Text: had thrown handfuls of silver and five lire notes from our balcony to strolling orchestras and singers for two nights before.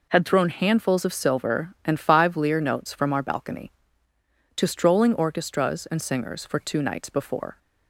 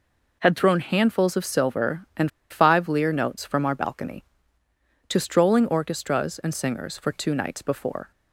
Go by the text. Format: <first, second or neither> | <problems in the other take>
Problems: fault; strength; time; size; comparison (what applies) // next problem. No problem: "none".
first | pauses between "and" and "five"; slight; at 2.3 s; 0.20 s long